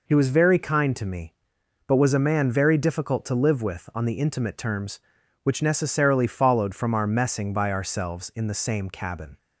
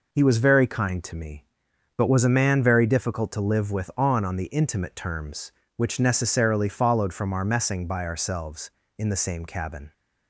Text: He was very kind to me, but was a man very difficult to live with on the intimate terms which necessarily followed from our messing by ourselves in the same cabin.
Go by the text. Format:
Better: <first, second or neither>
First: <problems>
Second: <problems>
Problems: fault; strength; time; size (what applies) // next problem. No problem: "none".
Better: first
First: none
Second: says "on" twice; at 4.2 s